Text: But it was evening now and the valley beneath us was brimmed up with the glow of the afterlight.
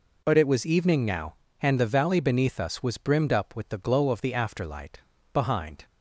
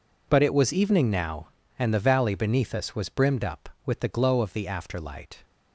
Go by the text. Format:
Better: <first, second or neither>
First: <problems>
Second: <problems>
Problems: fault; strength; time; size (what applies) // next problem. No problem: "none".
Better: second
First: goes on to say "Behind"; from 5.3 s on; 0.52 s long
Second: none